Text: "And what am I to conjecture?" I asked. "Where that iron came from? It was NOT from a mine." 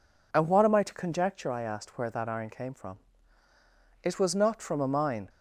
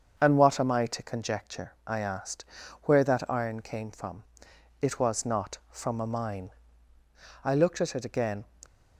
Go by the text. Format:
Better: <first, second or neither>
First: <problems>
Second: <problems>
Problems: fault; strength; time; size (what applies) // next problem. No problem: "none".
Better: first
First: none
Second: starts louder than the rest; until 1.2 s; 7 dB // goes on to say "I looked at it again"; noticeable; from 7.4 s on; 1.0 s long